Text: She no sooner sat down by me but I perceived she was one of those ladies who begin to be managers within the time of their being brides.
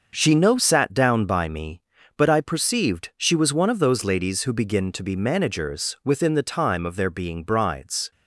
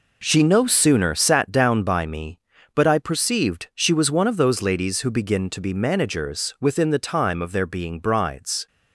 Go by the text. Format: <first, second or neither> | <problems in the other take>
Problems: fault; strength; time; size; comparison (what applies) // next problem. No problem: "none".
second | starts louder than the rest; until 1.1 s; 6 dB // skips "sooner"; at 0.5 s